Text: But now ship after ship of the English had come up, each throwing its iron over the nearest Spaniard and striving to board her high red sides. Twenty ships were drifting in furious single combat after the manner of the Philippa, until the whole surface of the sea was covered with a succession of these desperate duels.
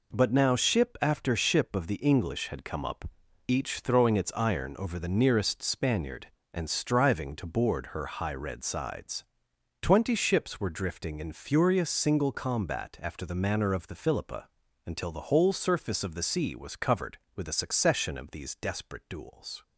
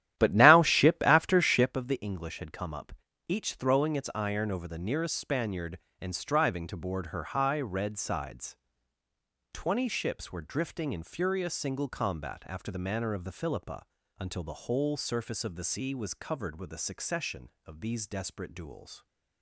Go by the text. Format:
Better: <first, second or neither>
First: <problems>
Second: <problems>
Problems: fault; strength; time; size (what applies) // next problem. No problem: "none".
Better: first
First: none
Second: starts louder than the rest; strong; until 1.8 s; 12 dB